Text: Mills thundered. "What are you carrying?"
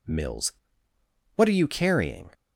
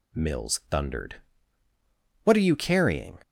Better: second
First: skips "thundered"; at 0.9 s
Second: none

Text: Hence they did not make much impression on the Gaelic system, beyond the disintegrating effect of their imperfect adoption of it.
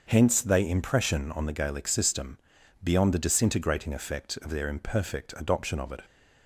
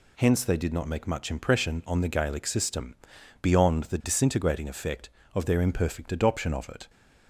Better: second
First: starts louder than the rest; until 1.0 s; 6.5 dB // skips "did not make much"; at 0.6 s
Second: none

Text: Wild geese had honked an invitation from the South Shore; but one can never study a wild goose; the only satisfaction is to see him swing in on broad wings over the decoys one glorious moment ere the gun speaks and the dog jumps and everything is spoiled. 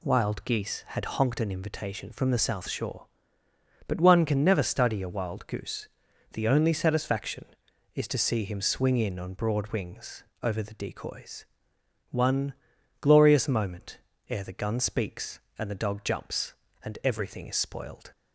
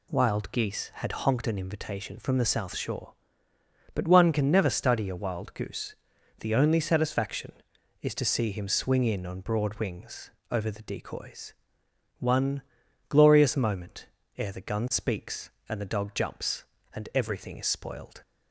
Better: neither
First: pauses between "wings" and "over"; slight; at 10.2 s; 0.16 s long // pauses between "decoys" and "one"; noticeable; at 11.4 s; 0.64 s long // pauses between "one" and "glorious"; noticeable; at 12.5 s; 0.46 s long // pauses between "moment" and "ere"; slight; at 13.9 s; 0.30 s long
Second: pauses between "wings" and "over"; slight; at 10.3 s; 0.18 s long // pauses between "decoys" and "one"; noticeable; at 11.5 s; 0.64 s long // pauses between "one" and "glorious"; noticeable; at 12.6 s; 0.46 s long // pauses between "moment" and "ere"; slight; at 14.0 s; 0.30 s long

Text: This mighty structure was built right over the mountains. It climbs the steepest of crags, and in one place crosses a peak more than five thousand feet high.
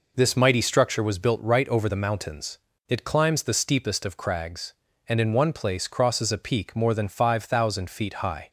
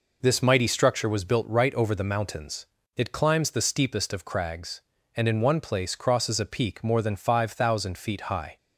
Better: neither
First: none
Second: none

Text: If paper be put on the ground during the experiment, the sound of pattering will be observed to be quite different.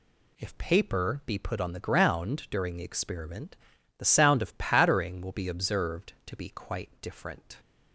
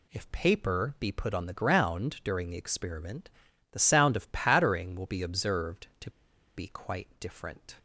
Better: first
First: none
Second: pauses between "to" and "be"; noticeable; at 6.0 s; 0.46 s long

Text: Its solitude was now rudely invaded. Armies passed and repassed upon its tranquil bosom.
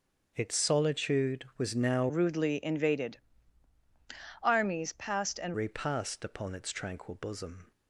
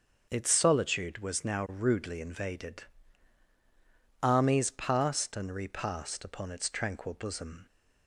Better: second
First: starts louder than the rest; until 1.3 s; 6 dB // changes voice from "rudely" to "and"; from 2.0 to 5.5 s; 3.5 s long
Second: starts louder than the rest; until 1.3 s; 6.5 dB

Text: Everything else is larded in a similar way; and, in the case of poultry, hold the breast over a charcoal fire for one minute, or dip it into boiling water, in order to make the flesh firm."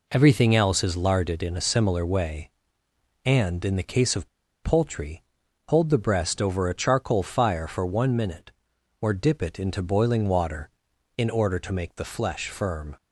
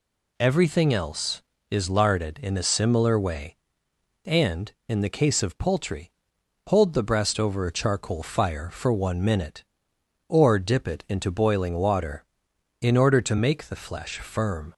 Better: second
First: pauses between "of" and "poultry"; slight; at 4.2 s; 0.36 s long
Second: none

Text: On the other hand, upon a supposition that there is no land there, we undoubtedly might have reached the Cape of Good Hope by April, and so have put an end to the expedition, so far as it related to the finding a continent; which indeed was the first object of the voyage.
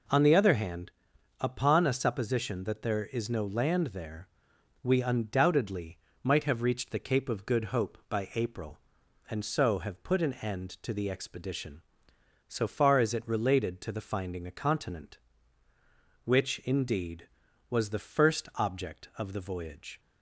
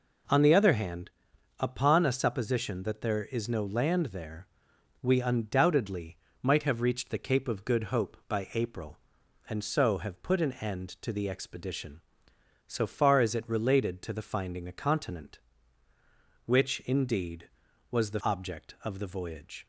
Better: first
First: pauses between "undoubtedly" and "might"; slight; at 5.9 s; 0.26 s long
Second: pauses between "undoubtedly" and "might"; slight; at 6.1 s; 0.26 s long // skips "first"; at 18.2 s

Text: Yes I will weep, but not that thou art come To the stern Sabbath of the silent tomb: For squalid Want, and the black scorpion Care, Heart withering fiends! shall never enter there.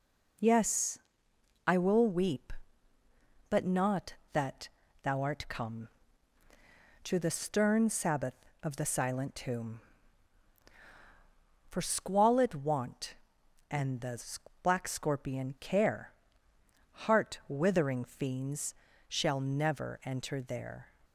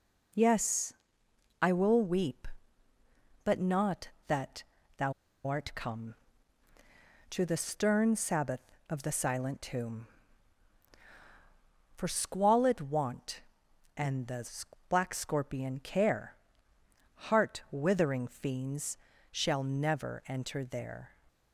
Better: first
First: pauses between "Yes" and "I"; noticeable; at 0.9 s; 0.68 s long // pauses between "that" and "thou"; slight; at 4.6 s; 0.34 s long // pauses between "the" and "black"; noticeable; at 14.1 s; 0.46 s long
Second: pauses between "Yes" and "I"; noticeable; at 0.9 s; 0.68 s long // pauses between "that" and "thou"; slight; at 4.6 s; 0.34 s long // pauses between "thou" and "art"; slight; at 5.1 s; 0.34 s long // pauses between "the" and "black"; noticeable; at 14.4 s; 0.46 s long

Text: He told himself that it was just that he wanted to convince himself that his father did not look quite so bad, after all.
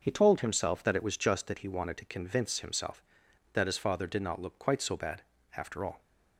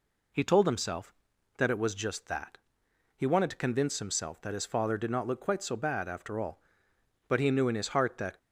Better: first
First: none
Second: pauses between "that" and "he"; noticeable; at 2.5 s; 0.58 s long // goes on to say "But he knew in his heart that"; noticeable; from 7.2 s on; 1.1 s long

